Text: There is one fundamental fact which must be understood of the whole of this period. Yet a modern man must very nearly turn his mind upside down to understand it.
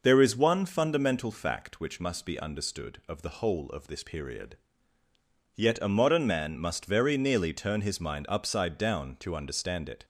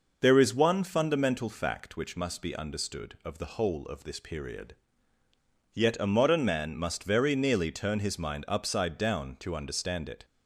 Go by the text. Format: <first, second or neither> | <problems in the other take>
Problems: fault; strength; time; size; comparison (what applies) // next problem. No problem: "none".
neither | none